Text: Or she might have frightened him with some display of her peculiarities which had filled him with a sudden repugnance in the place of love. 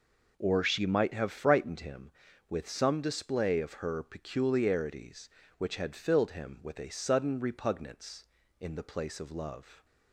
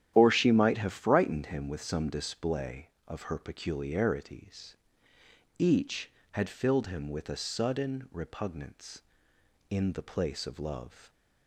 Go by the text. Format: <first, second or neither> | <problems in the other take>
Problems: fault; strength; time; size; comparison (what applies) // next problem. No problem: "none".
first | starts louder than the rest; strong; until 1.1 s; 11 dB // says "each" for "which"; at 5.5 s